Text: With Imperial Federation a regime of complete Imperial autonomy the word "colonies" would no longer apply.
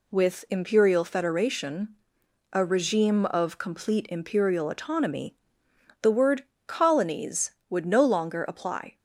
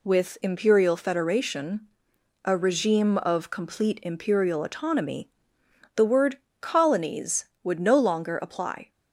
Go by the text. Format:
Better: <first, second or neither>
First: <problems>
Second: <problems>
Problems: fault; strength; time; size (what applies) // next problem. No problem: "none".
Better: neither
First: pauses between "Federation" and "a"; noticeable; at 1.8 s; 0.64 s long // pauses between "autonomy" and "the"; noticeable; at 5.3 s; 0.66 s long // pauses between "word" and "colonies"; slight; at 6.4 s; 0.24 s long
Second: pauses between "Federation" and "a"; noticeable; at 1.8 s; 0.64 s long // pauses between "autonomy" and "the"; noticeable; at 5.2 s; 0.66 s long // pauses between "word" and "colonies"; slight; at 6.3 s; 0.24 s long